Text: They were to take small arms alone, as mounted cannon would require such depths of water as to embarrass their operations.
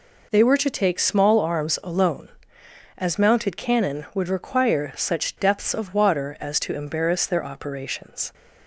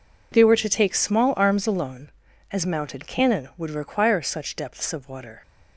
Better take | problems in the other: first | stops before "as to embarrass their operations"; at 5.4 s

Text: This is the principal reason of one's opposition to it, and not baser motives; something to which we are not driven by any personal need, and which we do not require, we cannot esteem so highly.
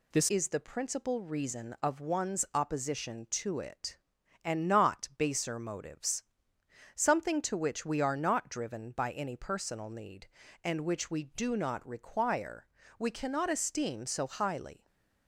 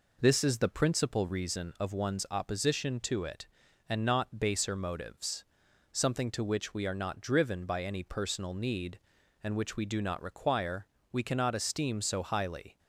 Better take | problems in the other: second | changes voice at "is"; from 0.2 s on; 14.6 s long // stays silent after the last word; slight; from 14.7 s on; 0.5 s long

